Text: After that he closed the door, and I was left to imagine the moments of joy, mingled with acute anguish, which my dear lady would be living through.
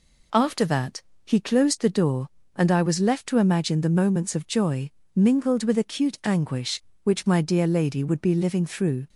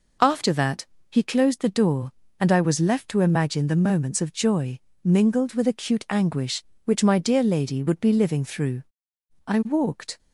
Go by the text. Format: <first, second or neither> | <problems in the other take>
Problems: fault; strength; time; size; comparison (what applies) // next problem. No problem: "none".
first | pauses between "that" and "he"; slight; at 0.8 s; 0.24 s long; slight in the first // goes on to say "I walked"; noticeable; from 9.4 s on; 0.72 s long